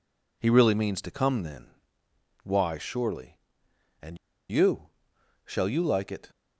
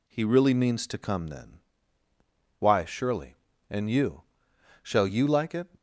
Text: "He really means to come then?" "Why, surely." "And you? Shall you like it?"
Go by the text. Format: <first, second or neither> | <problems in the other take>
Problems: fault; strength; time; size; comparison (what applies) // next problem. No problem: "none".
second | pauses between "And" and "you"; slight; at 4.1 s; 0.34 s long